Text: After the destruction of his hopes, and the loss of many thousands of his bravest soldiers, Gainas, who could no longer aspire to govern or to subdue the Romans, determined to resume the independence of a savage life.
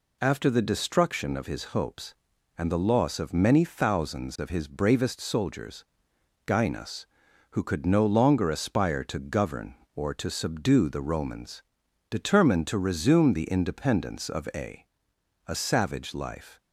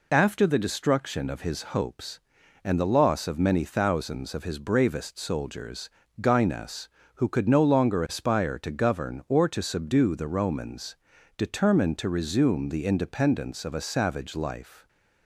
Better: second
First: says "a" twice; at 15.4 s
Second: none

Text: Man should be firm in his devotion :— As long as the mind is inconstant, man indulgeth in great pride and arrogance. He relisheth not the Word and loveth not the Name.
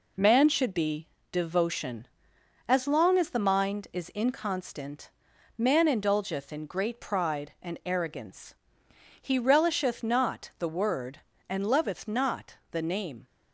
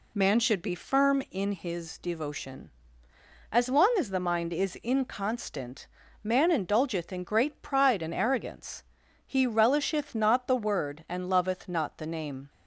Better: second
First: skips "firm in his"; at 1.1 s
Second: none

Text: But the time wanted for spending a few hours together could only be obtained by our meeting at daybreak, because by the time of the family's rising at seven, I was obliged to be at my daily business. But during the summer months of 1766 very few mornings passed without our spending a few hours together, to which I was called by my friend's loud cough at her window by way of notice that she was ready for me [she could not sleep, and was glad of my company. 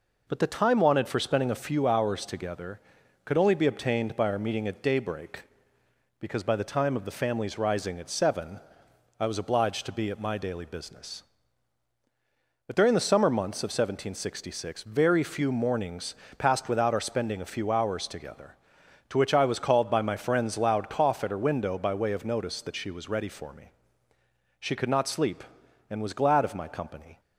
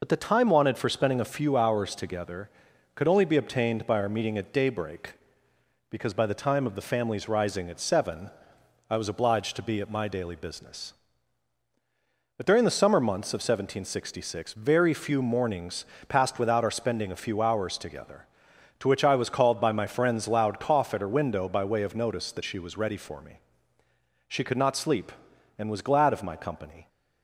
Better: first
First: pauses between "mornings" and "passed"; slight; at 16.1 s; 0.24 s long // pauses between "me" and "she"; noticeable; at 23.7 s; 0.88 s long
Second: loses the start of "But"; at 0.0 s; 45 ms // pauses between "mornings" and "passed"; slight; at 15.8 s; 0.24 s long // pauses between "me" and "she"; noticeable; at 23.3 s; 0.88 s long

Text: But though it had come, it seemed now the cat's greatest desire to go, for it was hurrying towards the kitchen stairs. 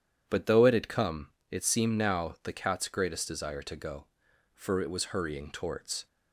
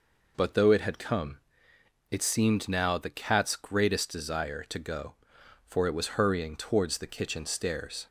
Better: second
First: starts louder than the rest; strong; until 1.2 s; 9.5 dB // stops before "the kitchen stairs"; at 6.0 s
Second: none

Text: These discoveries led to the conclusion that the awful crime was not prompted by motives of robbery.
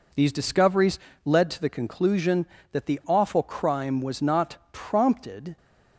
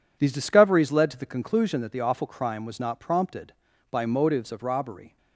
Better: second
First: pauses between "discoveries" and "led"; slight; at 0.9 s; 0.26 s long // pauses between "not" and "prompted"; slight; at 4.5 s; 0.16 s long // stops before "by motives of robbery"; at 5.5 s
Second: none

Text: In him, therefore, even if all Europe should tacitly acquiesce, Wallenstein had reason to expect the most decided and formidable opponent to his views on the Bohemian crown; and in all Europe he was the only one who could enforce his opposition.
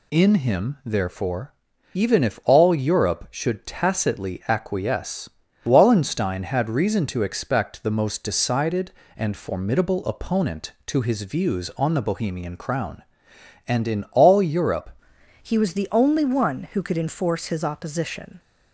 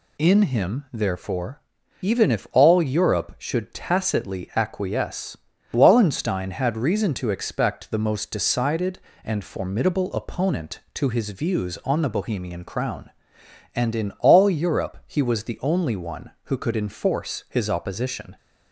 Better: second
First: changes voice at "he"; from 15.4 s on; 2.9 s long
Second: none

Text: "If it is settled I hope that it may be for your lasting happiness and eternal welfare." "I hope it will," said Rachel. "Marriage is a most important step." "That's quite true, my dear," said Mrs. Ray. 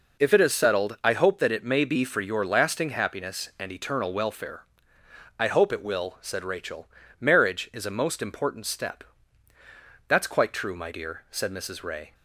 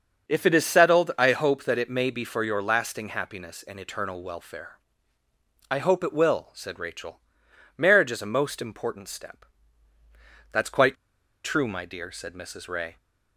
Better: first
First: none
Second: starts louder than the rest; strong; until 1.3 s; 7 dB // pauses between "quite" and "true"; noticeable; at 10.9 s; 0.48 s long

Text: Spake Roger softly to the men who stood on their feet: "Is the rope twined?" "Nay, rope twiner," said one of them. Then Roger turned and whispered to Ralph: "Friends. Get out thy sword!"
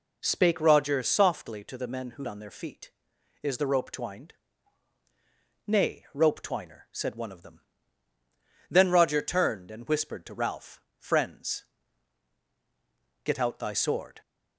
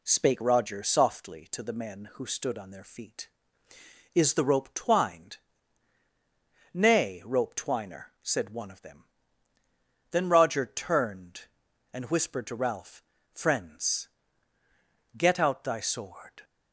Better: second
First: skips "stood"; at 2.2 s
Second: none

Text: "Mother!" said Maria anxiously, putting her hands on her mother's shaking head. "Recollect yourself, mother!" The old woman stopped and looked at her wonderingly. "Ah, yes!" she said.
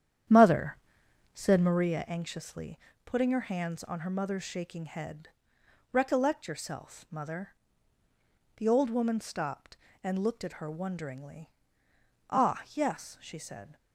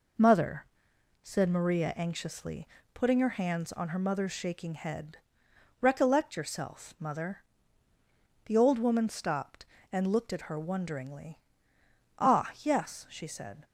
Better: second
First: starts louder than the rest; strong; until 2.0 s; 9.5 dB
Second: none

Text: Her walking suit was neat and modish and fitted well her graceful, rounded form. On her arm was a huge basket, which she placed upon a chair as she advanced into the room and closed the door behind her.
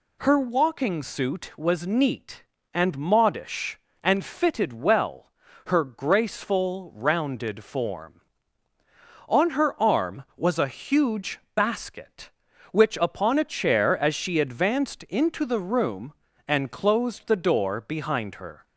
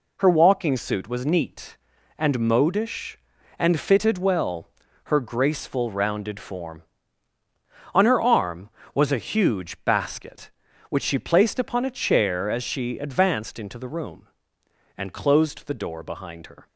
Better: second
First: pauses between "well" and "her"; slight; at 5.3 s; 0.36 s long // pauses between "huge" and "basket"; slight; at 11.3 s; 0.16 s long // skips "she placed"; at 12.9 s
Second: pauses between "well" and "her"; slight; at 4.6 s; 0.36 s long

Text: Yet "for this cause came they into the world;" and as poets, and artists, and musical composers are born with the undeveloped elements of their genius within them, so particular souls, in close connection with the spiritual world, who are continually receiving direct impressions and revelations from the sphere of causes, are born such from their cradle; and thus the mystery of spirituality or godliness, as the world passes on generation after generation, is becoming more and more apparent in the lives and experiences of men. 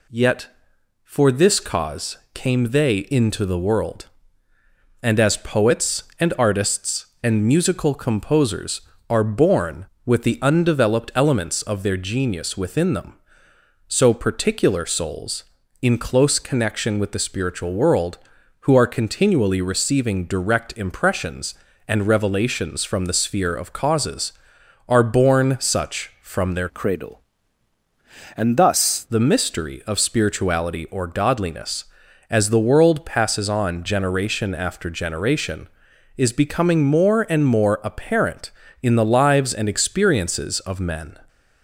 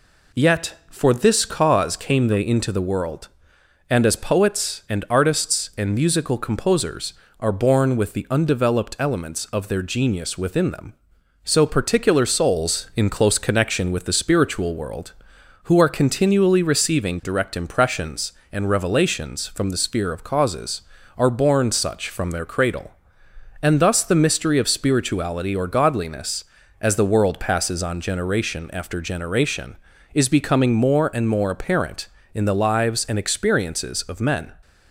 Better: second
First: pauses between "cause" and "came"; slight; at 2.1 s; 0.16 s long // changes voice from "cradle" to "thus"; from 26.6 to 29.0 s; 2.4 s long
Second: none

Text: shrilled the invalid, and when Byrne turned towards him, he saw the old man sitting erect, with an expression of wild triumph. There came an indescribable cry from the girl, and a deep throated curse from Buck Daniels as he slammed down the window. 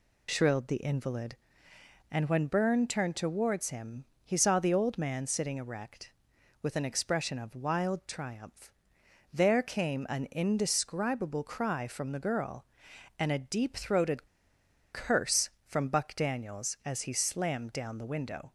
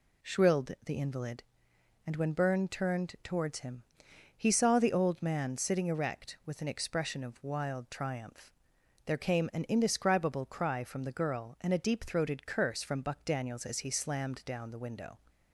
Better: second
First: pauses between "throated" and "curse"; noticeable; at 14.2 s; 0.65 s long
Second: none

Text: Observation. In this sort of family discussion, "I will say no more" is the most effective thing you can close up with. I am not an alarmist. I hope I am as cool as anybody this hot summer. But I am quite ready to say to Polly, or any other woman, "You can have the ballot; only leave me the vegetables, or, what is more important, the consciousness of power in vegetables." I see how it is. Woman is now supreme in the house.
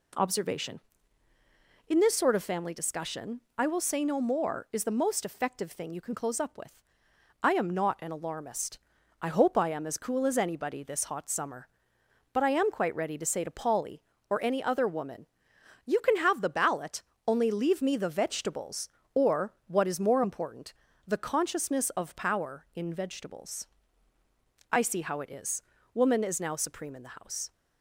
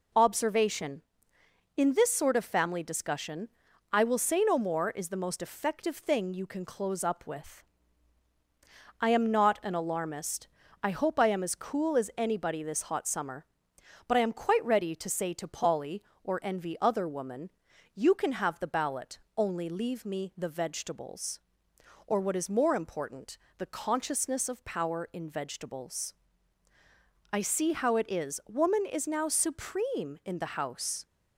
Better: first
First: none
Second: says "envy" for "any"; at 16.4 s

